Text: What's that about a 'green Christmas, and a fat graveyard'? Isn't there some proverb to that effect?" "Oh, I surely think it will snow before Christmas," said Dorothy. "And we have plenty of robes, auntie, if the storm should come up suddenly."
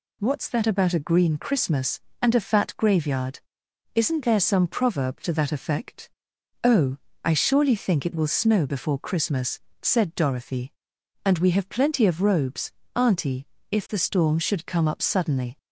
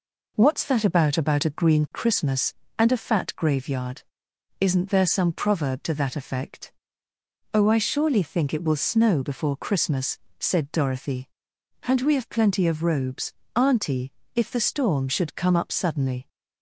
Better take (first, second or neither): first